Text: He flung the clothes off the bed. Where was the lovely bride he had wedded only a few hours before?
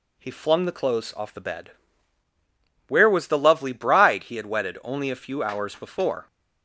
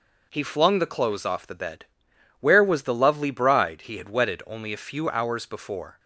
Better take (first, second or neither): neither